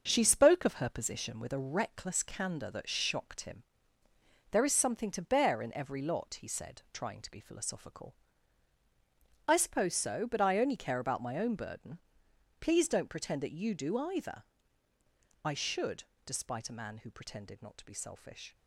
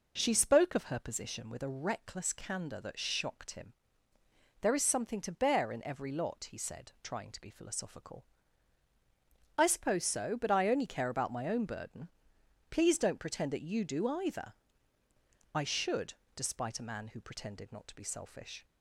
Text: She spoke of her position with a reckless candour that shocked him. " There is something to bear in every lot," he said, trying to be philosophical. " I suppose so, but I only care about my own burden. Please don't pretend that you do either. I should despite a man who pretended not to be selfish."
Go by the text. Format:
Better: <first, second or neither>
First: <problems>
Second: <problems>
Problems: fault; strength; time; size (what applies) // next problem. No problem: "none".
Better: second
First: gets quieter; noticeable; throughout; 4.5 dB // starts louder than the rest; strong; until 1.0 s; 8.5 dB // pauses between "should" and "despite"; slight; at 16.0 s; 0.20 s long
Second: starts louder than the rest; strong; until 1.1 s; 7.5 dB // pauses between "should" and "despite"; slight; at 16.1 s; 0.20 s long